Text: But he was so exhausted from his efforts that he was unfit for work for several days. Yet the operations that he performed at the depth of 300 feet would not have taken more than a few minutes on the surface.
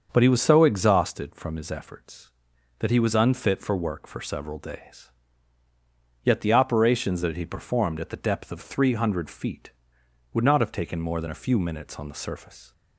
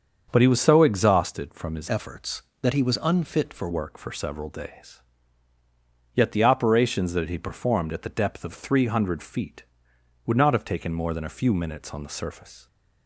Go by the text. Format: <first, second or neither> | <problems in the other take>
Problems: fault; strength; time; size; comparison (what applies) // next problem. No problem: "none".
first | starts louder than the rest; until 1.3 s; 7 dB; also in the first // changes voice from "efforts" to "for"; from 1.8 to 3.7 s; 1.9 s long